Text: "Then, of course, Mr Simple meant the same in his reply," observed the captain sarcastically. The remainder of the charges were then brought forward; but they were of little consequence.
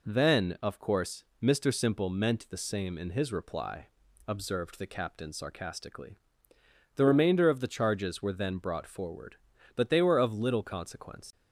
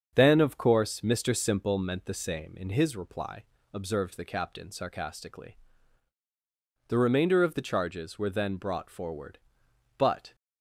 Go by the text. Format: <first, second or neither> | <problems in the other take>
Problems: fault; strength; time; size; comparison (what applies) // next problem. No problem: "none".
first | starts louder than the rest; strong; until 1.1 s; 7 dB // stops before "they were of little consequence"; at 10.3 s